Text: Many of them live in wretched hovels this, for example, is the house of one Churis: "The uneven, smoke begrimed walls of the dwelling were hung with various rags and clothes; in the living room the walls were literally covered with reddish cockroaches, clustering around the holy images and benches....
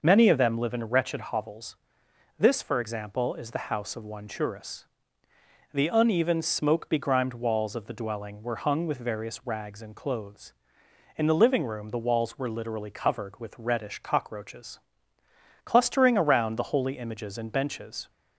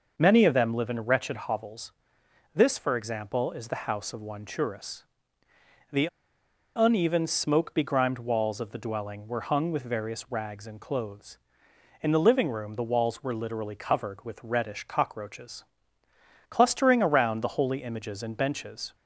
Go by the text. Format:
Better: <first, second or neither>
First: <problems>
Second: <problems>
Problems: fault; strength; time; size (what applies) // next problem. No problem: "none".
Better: first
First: pauses between "hovels" and "this"; noticeable; at 1.7 s; 0.64 s long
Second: pauses between "hovels" and "this"; noticeable; at 1.9 s; 0.64 s long // pauses between "The" and "uneven"; noticeable; at 6.0 s; 0.69 s long